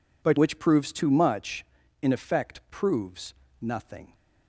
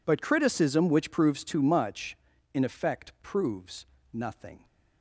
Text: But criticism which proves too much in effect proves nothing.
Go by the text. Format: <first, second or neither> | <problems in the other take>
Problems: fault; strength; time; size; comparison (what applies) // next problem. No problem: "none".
second | skips "criticism"; at 0.3 s // pauses between "proves" and "nothing"; slight; at 3.3 s; 0.26 s long; slight in the second